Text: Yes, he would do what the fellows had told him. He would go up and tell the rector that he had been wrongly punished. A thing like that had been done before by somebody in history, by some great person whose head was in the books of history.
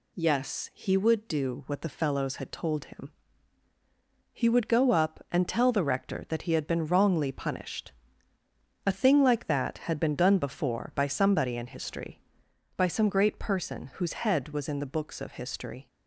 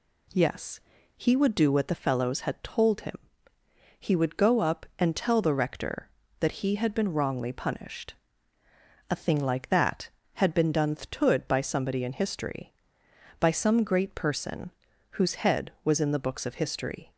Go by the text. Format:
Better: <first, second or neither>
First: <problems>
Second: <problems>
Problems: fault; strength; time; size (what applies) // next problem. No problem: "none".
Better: first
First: none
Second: says "thtood" for "before"; at 10.9 s // pauses between "person" and "whose"; at 14.7 s; 0.44 s long